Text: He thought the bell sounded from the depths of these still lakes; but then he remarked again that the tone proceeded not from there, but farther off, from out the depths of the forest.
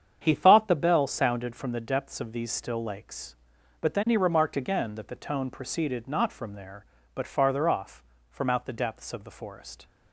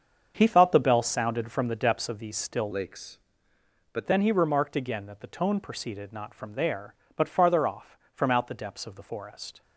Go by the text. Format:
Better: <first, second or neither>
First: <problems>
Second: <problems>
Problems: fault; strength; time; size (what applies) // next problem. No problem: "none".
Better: first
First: starts louder than the rest; strong; until 1.2 s; 8 dB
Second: starts louder than the rest; until 1.3 s; 7 dB // changes voice from "lakes" to "but"; from 2.7 to 4.0 s; 1.3 s long